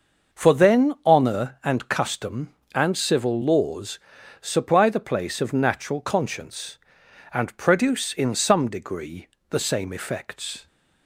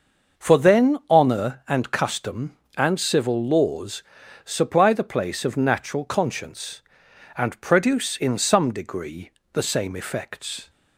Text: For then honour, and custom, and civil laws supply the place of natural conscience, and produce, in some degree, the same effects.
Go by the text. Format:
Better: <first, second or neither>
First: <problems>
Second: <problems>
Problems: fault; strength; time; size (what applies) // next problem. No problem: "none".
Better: neither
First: starts louder than the rest; until 1.4 s; 6 dB // pauses between "laws" and "supply"; at 3.9 s; 0.42 s long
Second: starts louder than the rest; noticeable; until 1.5 s; 6 dB // pauses between "laws" and "supply"; at 4.0 s; 0.42 s long